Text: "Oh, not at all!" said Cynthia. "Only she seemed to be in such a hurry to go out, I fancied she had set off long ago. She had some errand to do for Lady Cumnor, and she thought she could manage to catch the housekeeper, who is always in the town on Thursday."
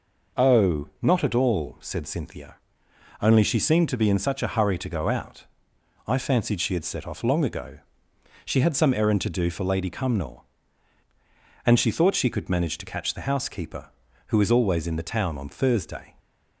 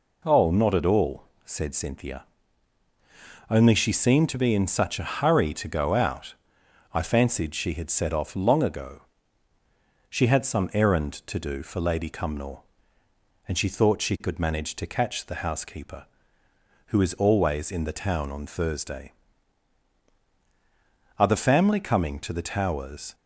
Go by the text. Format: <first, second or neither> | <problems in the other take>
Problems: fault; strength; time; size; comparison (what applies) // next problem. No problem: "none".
first | goes on to say "Are the family coming to the Towers"; strong; from 21.1 s on; 1.9 s long